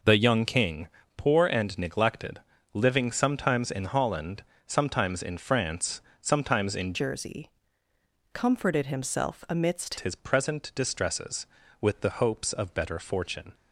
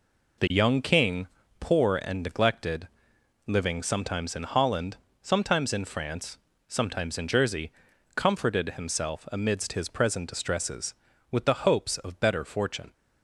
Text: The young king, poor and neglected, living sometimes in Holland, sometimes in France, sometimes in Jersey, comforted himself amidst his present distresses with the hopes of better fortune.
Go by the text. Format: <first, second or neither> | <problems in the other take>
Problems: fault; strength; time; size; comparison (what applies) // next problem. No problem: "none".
second | changes voice from "Jersey" to "amidst"; from 6.9 to 9.9 s; 3.0 s long